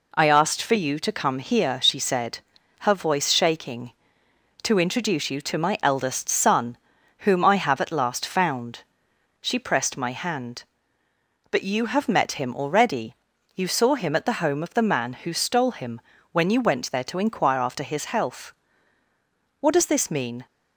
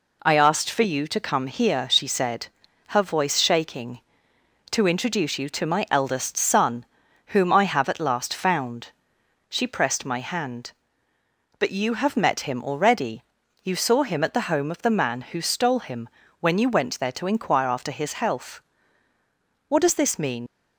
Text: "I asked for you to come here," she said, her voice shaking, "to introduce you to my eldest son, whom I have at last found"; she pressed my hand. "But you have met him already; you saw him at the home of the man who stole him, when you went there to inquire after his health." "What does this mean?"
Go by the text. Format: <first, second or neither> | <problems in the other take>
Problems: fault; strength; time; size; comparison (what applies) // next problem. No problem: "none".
first | leaves "mean" unfinished; at 20.4 s; 70 ms